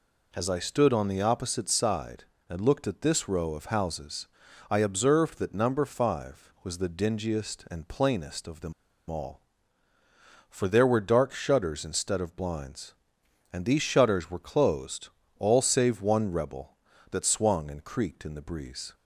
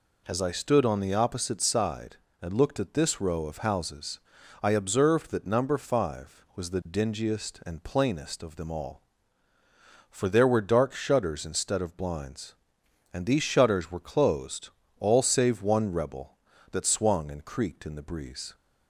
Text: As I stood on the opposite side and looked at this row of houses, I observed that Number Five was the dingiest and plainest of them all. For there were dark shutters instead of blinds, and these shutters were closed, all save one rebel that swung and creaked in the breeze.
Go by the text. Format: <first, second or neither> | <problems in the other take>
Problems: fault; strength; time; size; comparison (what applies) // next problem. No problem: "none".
second | pauses between "them" and "all"; slight; at 8.7 s; 0.35 s long